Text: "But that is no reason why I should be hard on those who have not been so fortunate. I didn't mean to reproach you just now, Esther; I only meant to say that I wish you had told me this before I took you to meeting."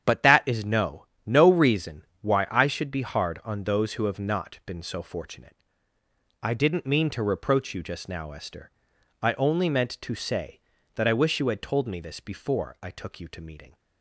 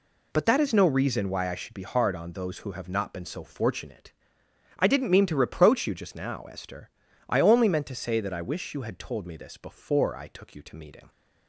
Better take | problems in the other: second | starts louder than the rest; strong; until 1.2 s; 8.5 dB // says "no" twice; at 1.2 s // pauses between "reason" and "why"; slight; at 2.0 s; 0.16 s long

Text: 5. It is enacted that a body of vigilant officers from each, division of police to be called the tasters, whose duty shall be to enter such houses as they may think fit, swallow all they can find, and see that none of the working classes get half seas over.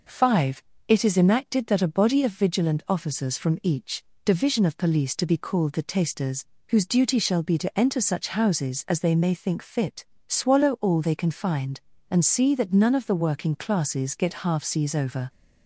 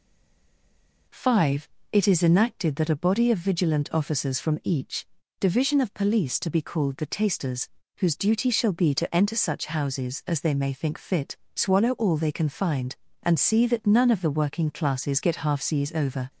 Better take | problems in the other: first | stays silent before the first word; until 1.0 s; 1.0 s long

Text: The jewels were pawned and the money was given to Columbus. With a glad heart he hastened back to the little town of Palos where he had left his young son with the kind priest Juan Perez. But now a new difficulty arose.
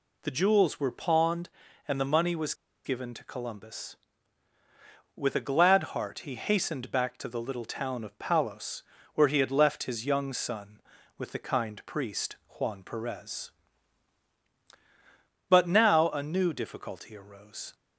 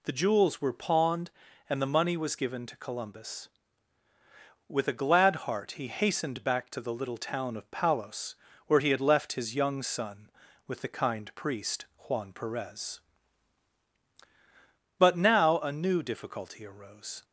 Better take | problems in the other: second | pauses between "was" and "given"; slight; at 2.5 s; 0.31 s long // pauses between "Palos" and "where"; slight; at 8.8 s; 0.32 s long; slight in the second

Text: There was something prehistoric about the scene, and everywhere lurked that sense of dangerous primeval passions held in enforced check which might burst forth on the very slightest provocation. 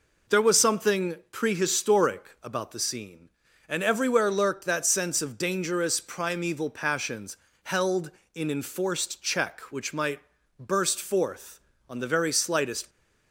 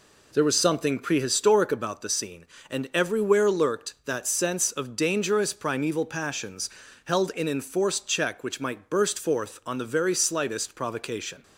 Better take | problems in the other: second | pauses between "something" and "prehistoric"; slight; at 1.1 s; 0.16 s long // pauses between "passions" and "held"; slight; at 7.3 s; 0.26 s long; slight in the second // pauses between "might" and "burst"; at 10.1 s; 0.40 s long // stops before "provocation"; at 12.8 s

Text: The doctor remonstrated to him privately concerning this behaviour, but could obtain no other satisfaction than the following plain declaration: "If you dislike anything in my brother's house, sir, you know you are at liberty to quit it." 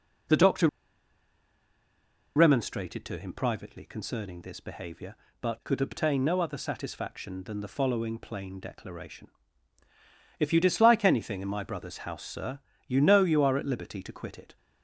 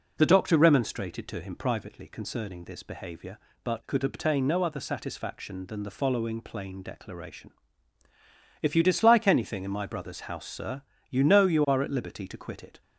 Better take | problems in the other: second | pauses between "doctor" and "remonstrated"; strong; at 0.6 s; 1.6 s long

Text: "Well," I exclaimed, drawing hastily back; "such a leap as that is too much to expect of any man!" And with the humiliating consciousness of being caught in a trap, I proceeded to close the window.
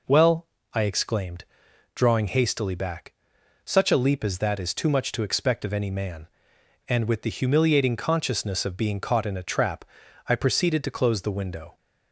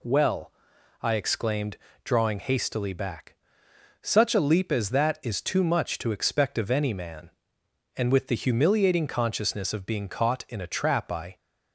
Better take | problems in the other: first | stops before "proceeded to close the window"; at 11.3 s

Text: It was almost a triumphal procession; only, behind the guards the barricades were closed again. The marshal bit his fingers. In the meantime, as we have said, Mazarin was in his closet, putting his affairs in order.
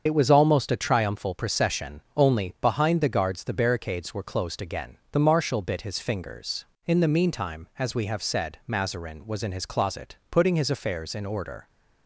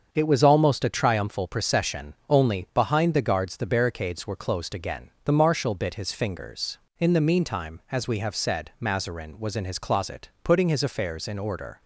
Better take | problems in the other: second | loses the start of "It"; at 0.0 s; 55 ms // starts louder than the rest; until 1.0 s; 7 dB; also in the second

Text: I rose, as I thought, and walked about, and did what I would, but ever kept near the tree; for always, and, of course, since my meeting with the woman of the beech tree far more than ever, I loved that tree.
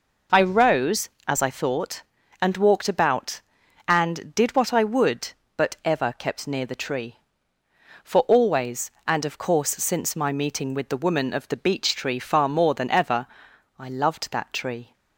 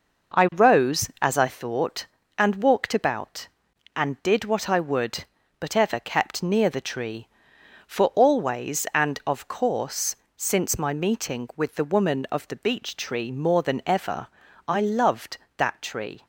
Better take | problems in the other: first | skips "far"; at 13.3 s

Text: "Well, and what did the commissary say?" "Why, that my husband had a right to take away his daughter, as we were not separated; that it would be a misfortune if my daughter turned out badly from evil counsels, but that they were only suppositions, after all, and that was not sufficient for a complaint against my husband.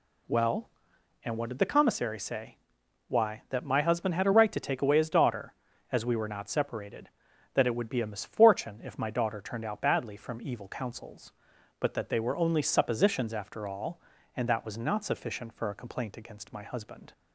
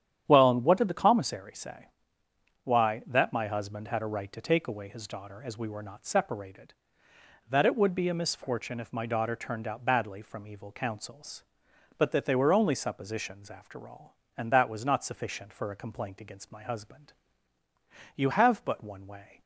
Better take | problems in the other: first | starts louder than the rest; strong; until 1.2 s; 10 dB // goes on to say "You have but one way"; noticeable; from 18.1 s on; 1.2 s long

